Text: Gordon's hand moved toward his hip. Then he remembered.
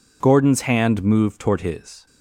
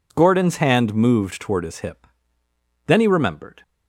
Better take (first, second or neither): second